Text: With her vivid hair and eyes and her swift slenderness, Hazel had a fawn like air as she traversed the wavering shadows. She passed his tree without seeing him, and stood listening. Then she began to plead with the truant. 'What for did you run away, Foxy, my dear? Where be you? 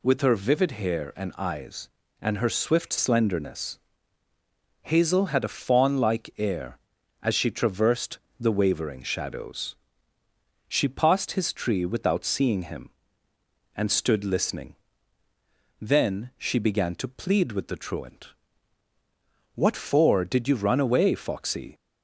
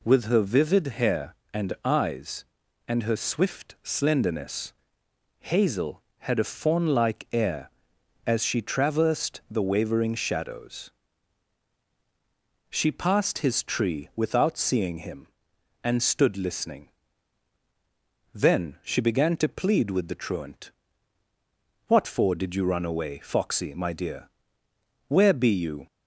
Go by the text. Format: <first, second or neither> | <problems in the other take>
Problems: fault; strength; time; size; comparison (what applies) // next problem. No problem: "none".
second | pauses between "traversed" and "the"; slight; at 8.1 s; 0.20 s long // stops before "my dear Where be you"; at 21.7 s